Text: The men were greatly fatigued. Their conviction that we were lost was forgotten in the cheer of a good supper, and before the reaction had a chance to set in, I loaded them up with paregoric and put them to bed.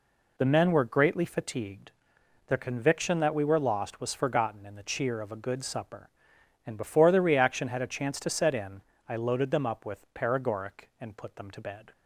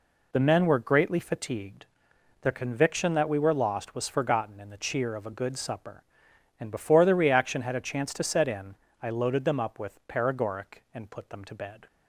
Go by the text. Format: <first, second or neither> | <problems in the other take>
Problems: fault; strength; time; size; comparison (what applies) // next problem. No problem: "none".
neither | none